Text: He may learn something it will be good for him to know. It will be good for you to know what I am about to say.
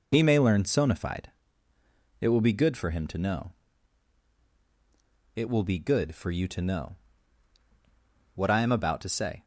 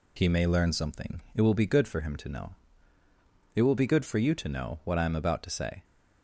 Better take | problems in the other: second | says "sonified" for "something"; at 0.6 s // pauses between "know" and "what"; strong; at 6.9 s; 1.4 s long

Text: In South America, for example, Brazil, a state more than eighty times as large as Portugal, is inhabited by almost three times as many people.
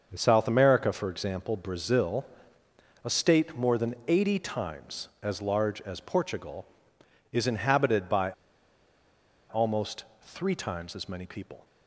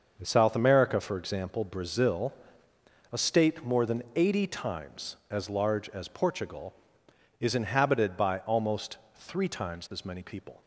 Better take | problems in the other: second | starts louder than the rest; until 1.1 s; 6.5 dB; also in the second // pauses between "by" and "almost"; at 8.3 s; 1.1 s long // pauses between "almost" and "three"; slight; at 10.0 s; 0.18 s long; slight in the second

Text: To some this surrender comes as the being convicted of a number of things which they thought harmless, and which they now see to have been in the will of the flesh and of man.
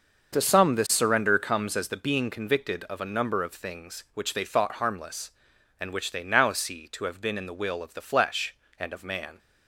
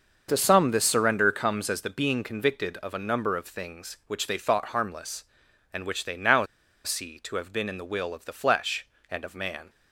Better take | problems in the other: first | starts louder than the rest; until 1.3 s; 6.5 dB; also in the first // pauses between "now" and "see"; at 6.4 s; 0.39 s long

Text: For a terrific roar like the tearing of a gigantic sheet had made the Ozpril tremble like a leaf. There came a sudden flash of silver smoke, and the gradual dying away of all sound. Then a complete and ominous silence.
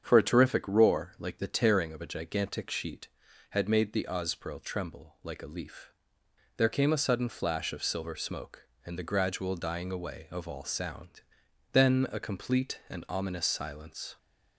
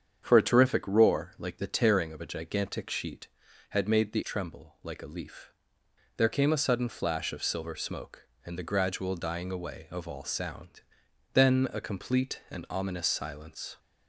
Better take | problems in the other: first | starts louder than the rest; strong; until 1.2 s; 7.5 dB; strong in the first // skips "Ozpril"; at 4.2 s

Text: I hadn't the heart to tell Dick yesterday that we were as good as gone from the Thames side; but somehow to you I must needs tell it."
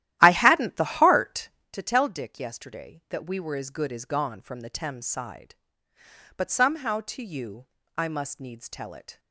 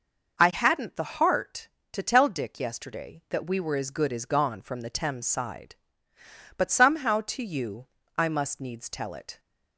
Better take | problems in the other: second | starts louder than the rest; strong; until 1.7 s; 13.5 dB // pauses between "you" and "I"; slight; at 7.6 s; 0.32 s long; slight in the second

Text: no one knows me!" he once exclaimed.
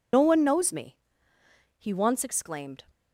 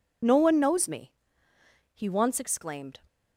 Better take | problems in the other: second | loses the start of "no"; at 0.1 s; 65 ms

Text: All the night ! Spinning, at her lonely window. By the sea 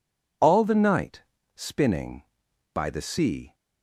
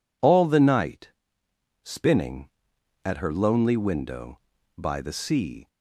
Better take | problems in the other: second | skips "at her lonely window"; at 2.4 s

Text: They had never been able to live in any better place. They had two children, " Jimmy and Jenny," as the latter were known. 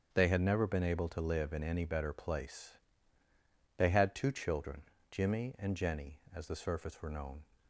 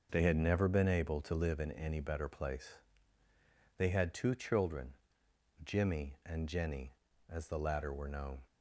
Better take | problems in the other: second | starts louder than the rest; strong; until 1.1 s; 7.5 dB; also in the second // says "surface" for "latter"; at 6.5 s

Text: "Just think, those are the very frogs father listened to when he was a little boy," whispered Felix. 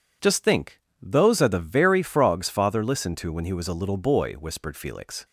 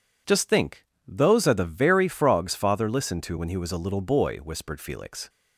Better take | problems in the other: neither | none

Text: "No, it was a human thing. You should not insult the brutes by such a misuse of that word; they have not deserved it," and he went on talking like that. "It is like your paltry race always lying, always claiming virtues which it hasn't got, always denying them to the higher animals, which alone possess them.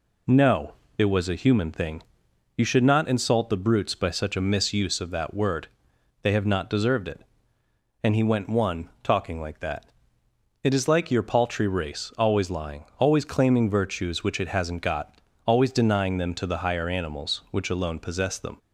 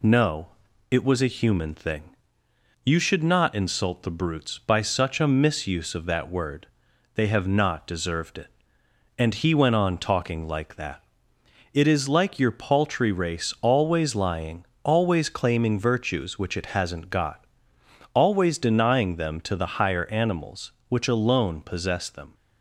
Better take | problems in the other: second | says "one" for "on"; at 8.4 s

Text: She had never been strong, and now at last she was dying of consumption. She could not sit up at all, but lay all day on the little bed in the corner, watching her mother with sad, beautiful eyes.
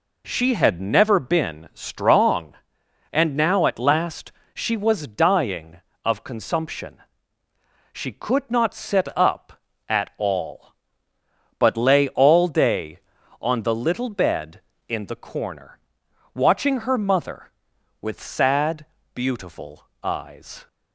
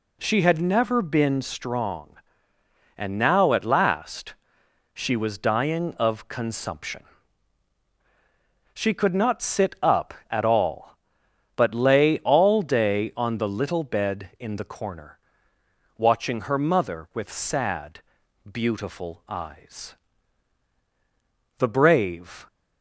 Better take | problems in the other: first | pauses between "last" and "she"; noticeable; at 4.3 s; 0.60 s long; slight in the first // goes on to say "The brave"; noticeable; from 21.5 s on; 0.88 s long

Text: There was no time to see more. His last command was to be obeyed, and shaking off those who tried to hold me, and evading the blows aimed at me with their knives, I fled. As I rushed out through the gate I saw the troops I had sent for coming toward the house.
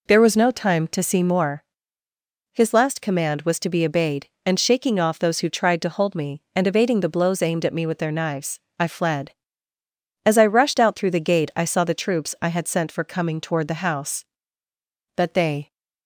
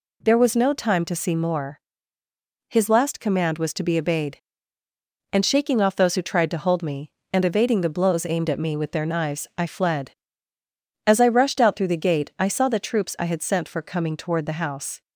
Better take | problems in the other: second | goes on to say "But they"; from 15.1 s on; 0.58 s long

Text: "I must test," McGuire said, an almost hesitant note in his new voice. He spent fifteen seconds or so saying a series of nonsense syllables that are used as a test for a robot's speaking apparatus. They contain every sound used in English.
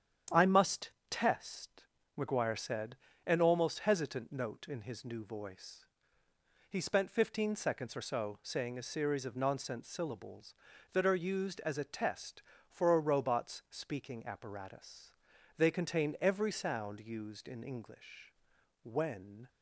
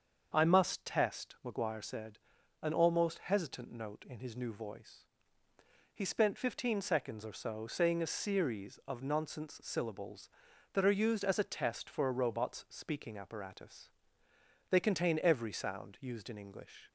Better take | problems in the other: second | starts louder than the rest; strong; until 1.4 s; 9 dB; also in the second // pauses between "must" and "test"; slight; at 0.9 s; 0.18 s long // goes on to say "When"; noticeable; from 18.8 s on; 0.66 s long

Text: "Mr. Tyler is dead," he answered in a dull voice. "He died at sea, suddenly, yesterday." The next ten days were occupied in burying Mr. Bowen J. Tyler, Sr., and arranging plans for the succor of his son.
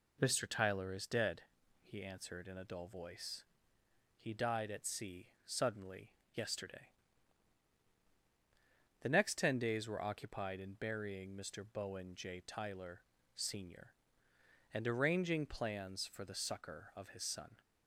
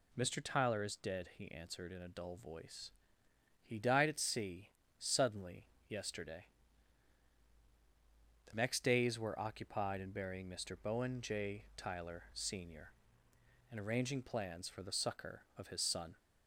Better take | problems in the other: first | skips "ten"; at 8.8 s

